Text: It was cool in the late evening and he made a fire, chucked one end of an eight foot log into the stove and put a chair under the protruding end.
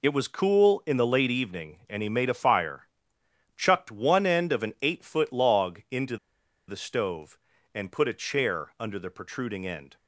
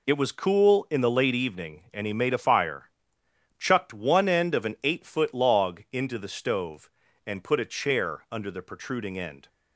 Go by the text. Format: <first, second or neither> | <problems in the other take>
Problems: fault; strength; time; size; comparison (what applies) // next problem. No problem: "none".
second | pauses between "into" and "the"; noticeable; at 6.1 s; 0.51 s long